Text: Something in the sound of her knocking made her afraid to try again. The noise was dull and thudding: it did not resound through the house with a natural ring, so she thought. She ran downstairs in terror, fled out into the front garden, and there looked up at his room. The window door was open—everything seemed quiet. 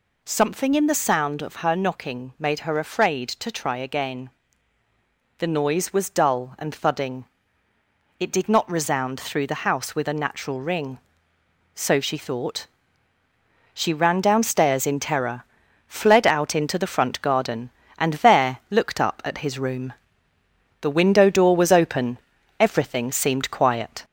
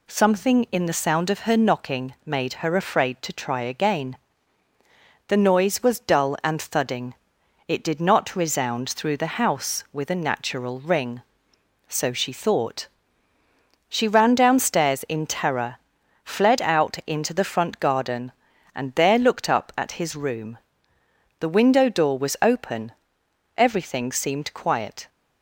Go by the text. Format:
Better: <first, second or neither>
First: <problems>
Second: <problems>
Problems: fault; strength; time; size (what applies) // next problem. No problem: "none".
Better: second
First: gets louder; slight; throughout; 2.5 dB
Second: none